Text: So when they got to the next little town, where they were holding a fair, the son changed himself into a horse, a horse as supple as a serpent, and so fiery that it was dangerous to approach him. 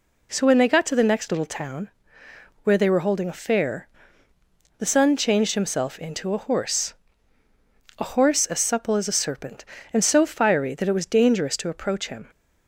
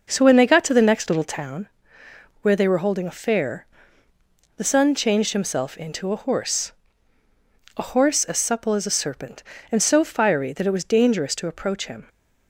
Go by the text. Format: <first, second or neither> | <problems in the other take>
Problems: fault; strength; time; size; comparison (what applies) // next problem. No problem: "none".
first | starts louder than the rest; noticeable; until 1.5 s; 5.5 dB